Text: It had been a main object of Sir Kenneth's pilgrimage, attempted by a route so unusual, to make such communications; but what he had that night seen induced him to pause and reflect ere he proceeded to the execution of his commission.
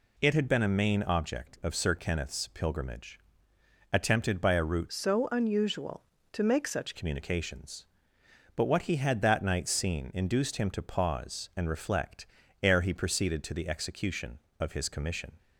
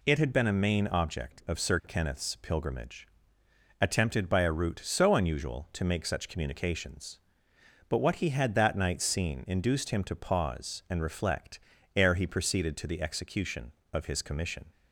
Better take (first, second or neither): second